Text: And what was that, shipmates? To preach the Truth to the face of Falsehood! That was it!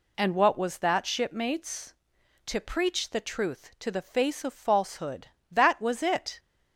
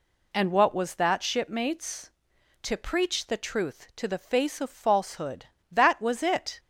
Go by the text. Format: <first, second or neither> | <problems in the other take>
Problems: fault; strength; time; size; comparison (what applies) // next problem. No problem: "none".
neither | none